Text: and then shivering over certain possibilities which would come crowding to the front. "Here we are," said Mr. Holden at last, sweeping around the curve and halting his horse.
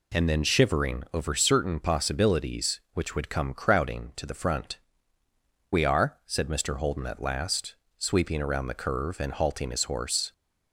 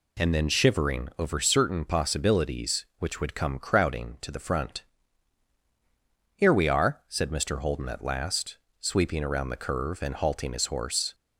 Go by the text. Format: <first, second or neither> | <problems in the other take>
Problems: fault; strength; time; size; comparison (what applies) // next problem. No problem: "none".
second | skips "Here"; at 5.2 s